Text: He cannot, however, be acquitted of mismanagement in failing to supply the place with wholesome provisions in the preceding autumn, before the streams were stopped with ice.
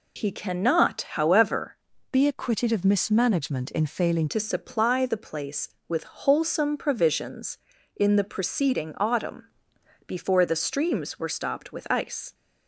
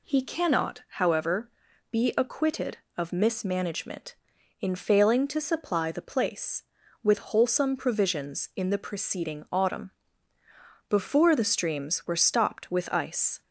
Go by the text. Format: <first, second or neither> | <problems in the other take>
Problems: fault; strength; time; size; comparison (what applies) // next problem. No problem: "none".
second | changes voice from "be" to "failing"; from 2.1 to 4.2 s; 2.1 s long